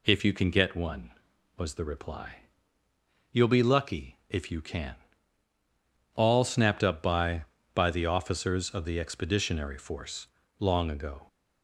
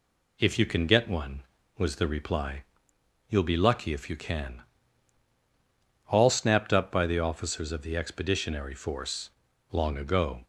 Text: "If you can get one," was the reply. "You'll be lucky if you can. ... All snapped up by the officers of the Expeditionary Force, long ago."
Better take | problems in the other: second | says "by" twice; at 7.7 s

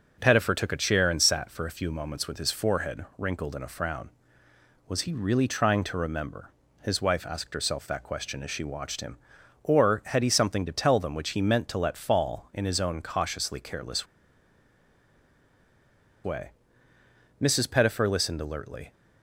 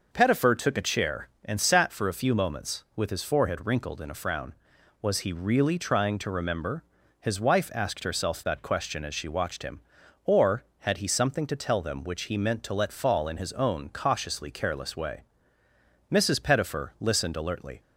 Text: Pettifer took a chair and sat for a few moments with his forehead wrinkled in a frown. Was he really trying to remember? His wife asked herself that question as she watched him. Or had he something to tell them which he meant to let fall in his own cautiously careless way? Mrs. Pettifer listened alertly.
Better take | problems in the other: second | pauses between "careless" and "way"; strong; at 14.0 s; 2.1 s long

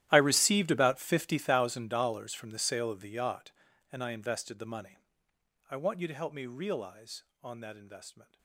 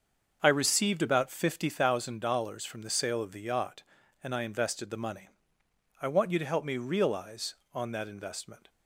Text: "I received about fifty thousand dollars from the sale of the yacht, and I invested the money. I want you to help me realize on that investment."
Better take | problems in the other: second | gets quieter; strong; throughout; 20.5 dB // starts louder than the rest; strong; until 1.1 s; 13 dB; also in the second

